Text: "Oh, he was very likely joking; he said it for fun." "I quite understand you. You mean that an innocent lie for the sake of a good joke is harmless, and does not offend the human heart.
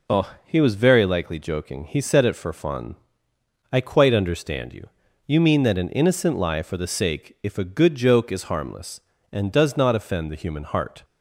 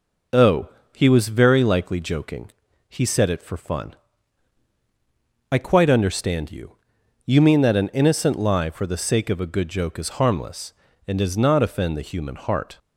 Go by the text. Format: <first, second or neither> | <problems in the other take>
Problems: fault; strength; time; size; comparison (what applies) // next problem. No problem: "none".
second | says "if" for "of"; at 7.4 s